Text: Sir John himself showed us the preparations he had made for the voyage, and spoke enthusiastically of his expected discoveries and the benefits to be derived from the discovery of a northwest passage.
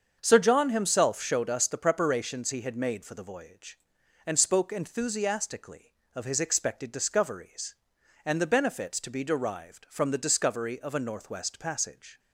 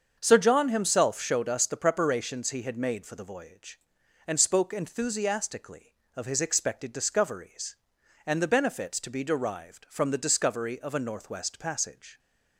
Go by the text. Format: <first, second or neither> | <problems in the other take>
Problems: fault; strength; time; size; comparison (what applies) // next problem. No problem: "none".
neither | starts louder than the rest; the same in both